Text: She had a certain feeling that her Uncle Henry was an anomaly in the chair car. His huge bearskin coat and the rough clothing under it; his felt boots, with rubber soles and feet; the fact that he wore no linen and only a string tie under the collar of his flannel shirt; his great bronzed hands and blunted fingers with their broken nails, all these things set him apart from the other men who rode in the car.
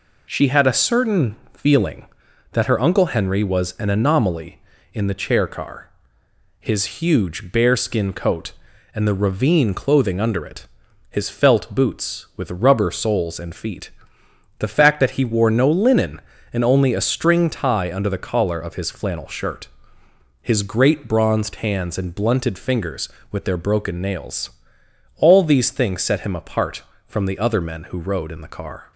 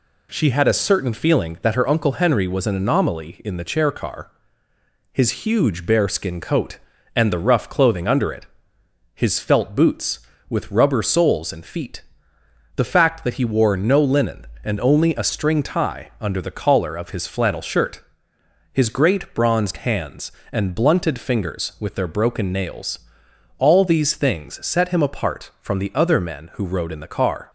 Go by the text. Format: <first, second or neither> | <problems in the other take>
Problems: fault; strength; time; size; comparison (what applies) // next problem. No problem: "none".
second | pauses between "certain" and "feeling"; slight; at 1.3 s; 0.18 s long // says "ravine" for "rough"; at 9.1 s